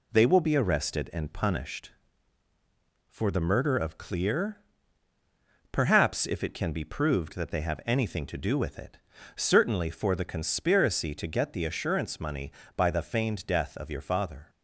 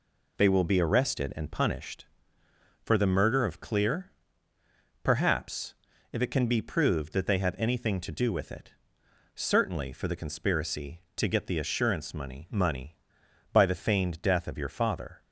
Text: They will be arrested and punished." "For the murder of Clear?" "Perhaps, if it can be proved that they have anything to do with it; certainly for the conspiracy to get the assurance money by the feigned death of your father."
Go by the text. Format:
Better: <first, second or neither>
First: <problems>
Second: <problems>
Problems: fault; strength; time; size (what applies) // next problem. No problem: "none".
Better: first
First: none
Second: says "money" twice; at 12.4 s